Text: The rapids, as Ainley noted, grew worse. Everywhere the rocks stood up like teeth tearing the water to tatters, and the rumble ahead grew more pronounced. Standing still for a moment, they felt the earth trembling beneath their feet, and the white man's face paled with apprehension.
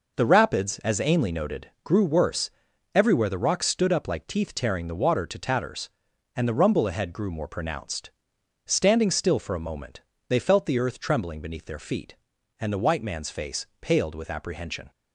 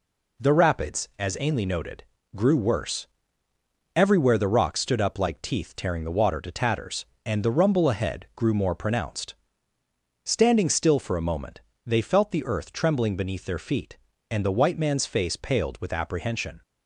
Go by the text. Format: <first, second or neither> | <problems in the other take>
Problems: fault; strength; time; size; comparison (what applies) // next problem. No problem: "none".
neither | none